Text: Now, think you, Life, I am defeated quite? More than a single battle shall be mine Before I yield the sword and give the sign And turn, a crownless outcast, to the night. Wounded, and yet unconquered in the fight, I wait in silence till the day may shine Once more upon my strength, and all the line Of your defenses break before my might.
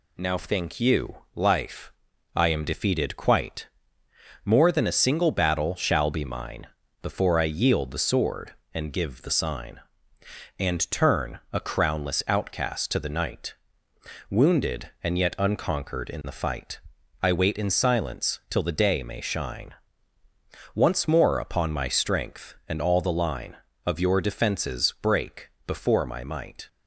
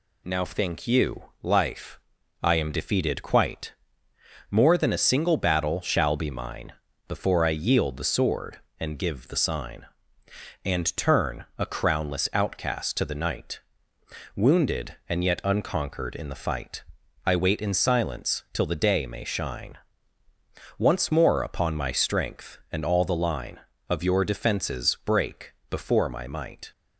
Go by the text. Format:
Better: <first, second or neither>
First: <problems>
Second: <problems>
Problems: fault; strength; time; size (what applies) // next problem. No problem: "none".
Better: neither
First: pauses between "mine" and "Before"; slight; at 6.6 s; 0.36 s long // pauses between "shine" and "Once"; at 19.7 s; 1.0 s long // pauses between "break" and "before"; slight; at 25.4 s; 0.16 s long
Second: pauses between "mine" and "Before"; slight; at 6.7 s; 0.36 s long // pauses between "shine" and "Once"; at 19.7 s; 1.0 s long // pauses between "break" and "before"; slight; at 25.5 s; 0.16 s long